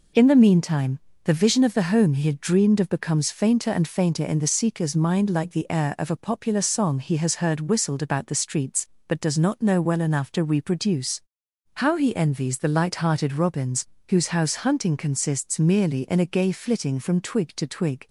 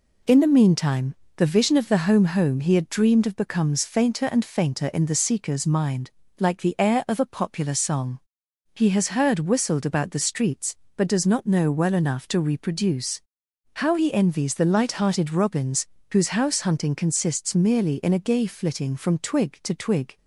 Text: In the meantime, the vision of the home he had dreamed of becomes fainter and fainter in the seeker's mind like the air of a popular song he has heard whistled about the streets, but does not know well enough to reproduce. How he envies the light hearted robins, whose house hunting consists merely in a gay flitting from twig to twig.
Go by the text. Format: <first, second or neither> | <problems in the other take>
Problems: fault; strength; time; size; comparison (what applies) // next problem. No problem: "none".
first | says "home" twice; at 2.2 s // pauses between "mind" and "like"; slight; at 6.1 s; 0.28 s long // pauses between "song" and "he"; noticeable; at 8.1 s; 0.56 s long